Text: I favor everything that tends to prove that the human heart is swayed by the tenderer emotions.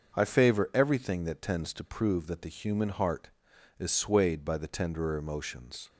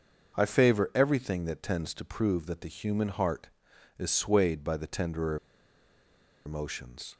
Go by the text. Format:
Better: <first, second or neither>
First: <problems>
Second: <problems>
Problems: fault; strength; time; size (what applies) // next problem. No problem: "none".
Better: first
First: starts louder than the rest; noticeable; until 1.2 s; 6 dB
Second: starts louder than the rest; noticeable; until 1.4 s; 6 dB // pauses between "tenderer" and "emotions"; at 5.3 s; 1.0 s long